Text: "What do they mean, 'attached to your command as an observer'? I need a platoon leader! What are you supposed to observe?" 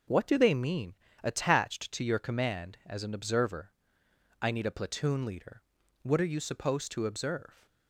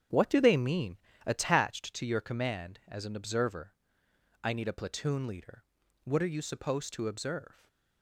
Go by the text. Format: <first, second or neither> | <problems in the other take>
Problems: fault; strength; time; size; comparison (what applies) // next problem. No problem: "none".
first | starts louder than the rest; strong; until 1.7 s; 8.5 dB // stays silent after the last word; slight; from 7.5 s on; 0.5 s long